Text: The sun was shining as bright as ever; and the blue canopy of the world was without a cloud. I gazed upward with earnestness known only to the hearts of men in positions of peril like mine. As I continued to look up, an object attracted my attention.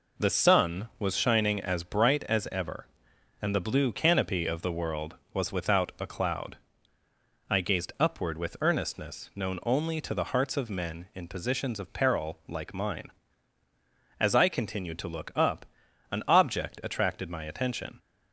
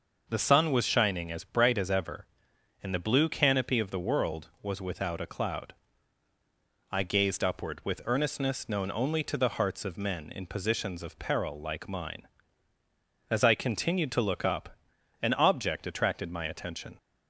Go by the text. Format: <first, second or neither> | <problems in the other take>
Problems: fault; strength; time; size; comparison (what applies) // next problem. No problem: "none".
neither | none